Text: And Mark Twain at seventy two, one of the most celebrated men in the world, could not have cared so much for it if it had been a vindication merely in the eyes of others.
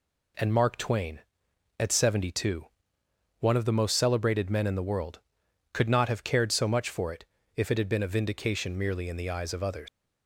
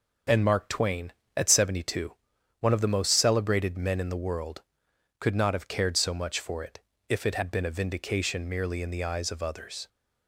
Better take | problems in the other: second | pauses between "it" and "if"; slight; at 7.2 s; 0.32 s long; slight in the second // leaves "others" unfinished; at 9.8 s; 95 ms

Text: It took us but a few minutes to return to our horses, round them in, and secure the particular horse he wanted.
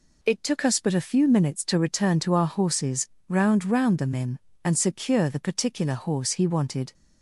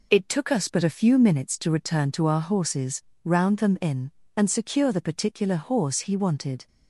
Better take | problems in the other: second | says "round" twice; at 3.6 s

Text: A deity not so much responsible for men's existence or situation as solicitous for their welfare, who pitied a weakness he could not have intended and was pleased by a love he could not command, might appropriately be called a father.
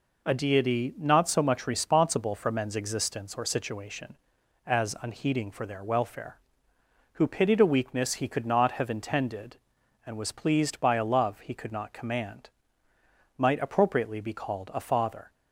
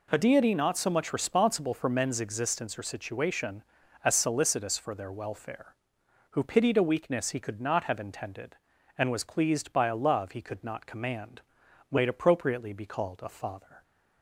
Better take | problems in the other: second | says "unheeding" for "solicitous"; at 5.0 s

